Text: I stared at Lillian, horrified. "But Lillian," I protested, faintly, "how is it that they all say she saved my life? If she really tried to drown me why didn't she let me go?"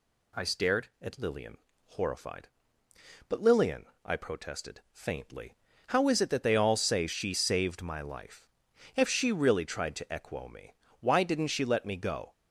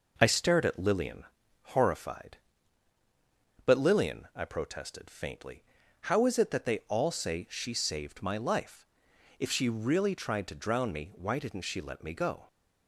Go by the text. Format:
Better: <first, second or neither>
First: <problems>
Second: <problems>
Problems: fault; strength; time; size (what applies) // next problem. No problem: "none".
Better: second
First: says "equo" for "drown"; at 10.0 s // pauses between "me" and "why"; slight; at 10.7 s; 0.30 s long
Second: none